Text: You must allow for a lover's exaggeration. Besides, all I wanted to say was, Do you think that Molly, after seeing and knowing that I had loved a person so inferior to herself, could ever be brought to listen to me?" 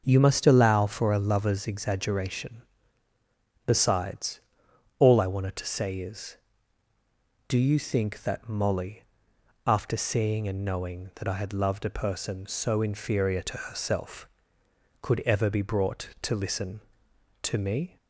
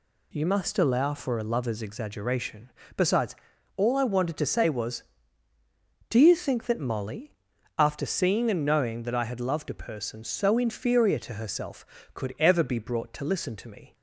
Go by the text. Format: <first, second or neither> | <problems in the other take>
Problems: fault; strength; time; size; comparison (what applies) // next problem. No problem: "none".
second | starts louder than the rest; until 1.0 s; 6.5 dB // says "is" for "was"; at 5.9 s